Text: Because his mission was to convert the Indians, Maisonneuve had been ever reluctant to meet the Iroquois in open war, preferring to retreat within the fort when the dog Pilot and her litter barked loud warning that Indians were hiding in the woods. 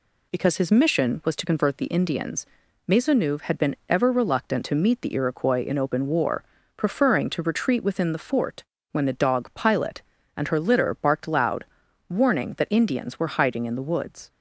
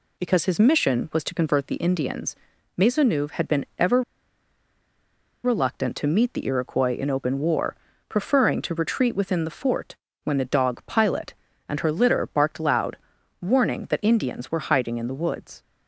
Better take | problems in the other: first | pauses between "ever" and "reluctant"; strong; at 4.0 s; 1.4 s long // pauses between "fort" and "when"; slight; at 9.9 s; 0.28 s long; slight in the first // pauses between "loud" and "warning"; at 12.9 s; 0.44 s long; also in the first

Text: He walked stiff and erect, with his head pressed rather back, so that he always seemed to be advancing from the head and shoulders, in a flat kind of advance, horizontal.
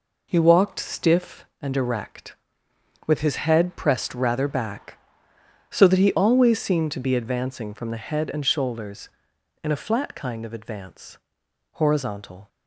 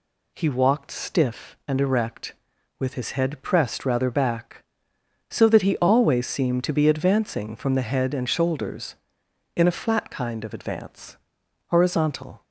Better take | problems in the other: neither | none

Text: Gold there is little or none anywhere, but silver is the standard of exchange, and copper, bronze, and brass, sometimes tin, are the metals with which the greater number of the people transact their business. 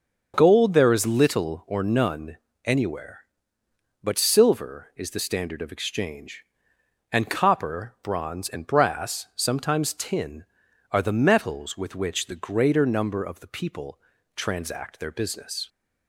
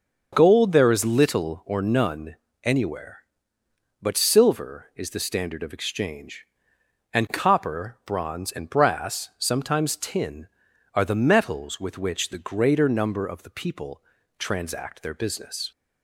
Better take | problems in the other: neither | starts louder than the rest; the same in both // pauses between "none" and "anywhere"; slight; the same in both // pauses between "people" and "transact"; slight; the same in both

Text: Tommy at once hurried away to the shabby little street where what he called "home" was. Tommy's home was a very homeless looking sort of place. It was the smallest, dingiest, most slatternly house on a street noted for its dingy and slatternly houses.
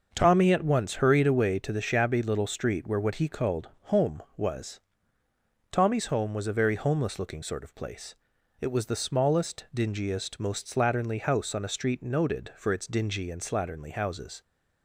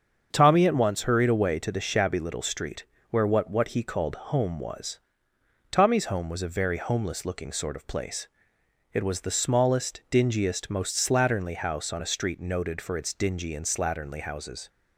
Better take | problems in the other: first | starts louder than the rest; until 1.3 s; 7 dB; also in the first // pauses between "street" and "where"; slight; at 2.8 s; 0.26 s long // says "what" twice; at 3.5 s

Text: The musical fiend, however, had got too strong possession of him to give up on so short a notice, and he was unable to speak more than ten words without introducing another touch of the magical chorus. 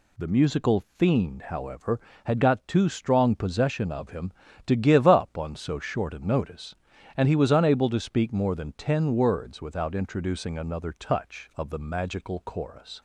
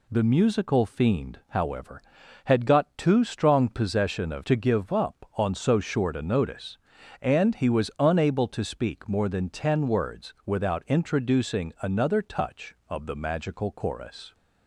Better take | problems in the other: first | skips "him"; at 4.4 s

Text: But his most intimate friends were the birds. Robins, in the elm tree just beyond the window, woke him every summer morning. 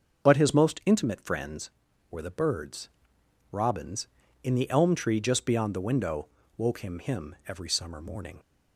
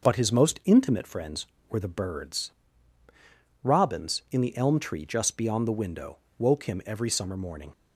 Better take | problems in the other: second | starts louder than the rest; until 1.3 s; 6.5 dB // says "him" twice; at 6.9 s

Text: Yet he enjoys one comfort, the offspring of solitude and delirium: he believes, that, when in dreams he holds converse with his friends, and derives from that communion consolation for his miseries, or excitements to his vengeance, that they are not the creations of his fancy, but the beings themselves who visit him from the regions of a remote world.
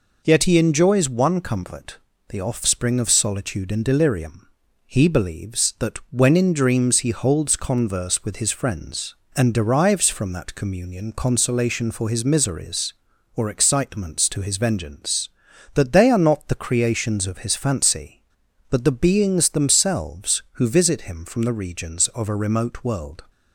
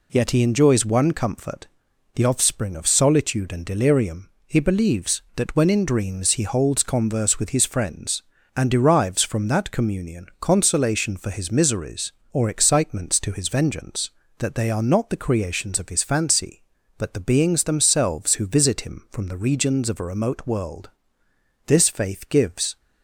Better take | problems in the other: first | goes on to say "This faith gives"; noticeable; from 21.6 s on; 1.1 s long

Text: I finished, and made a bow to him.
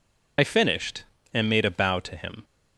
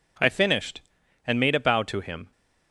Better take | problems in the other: second | loses the start of "I"; at 0.3 s; 40 ms

